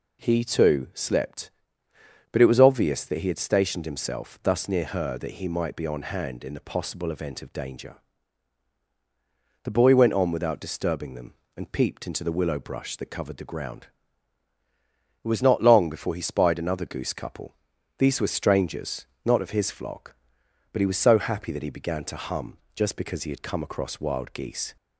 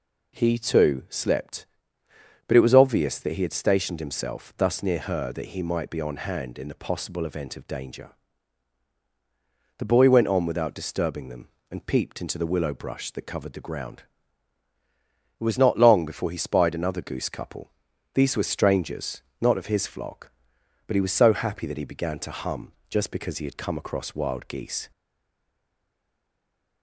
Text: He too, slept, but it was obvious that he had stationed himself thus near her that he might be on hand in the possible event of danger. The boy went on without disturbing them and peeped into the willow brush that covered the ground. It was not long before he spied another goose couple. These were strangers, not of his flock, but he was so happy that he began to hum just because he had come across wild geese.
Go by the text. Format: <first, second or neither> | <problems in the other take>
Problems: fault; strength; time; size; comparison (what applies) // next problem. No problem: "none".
first | pauses between "hum" and "just"; slight; at 22.7 s; 0.18 s long; slight in the first // stays silent after the last word; noticeable; from 24.9 s on; 1.9 s long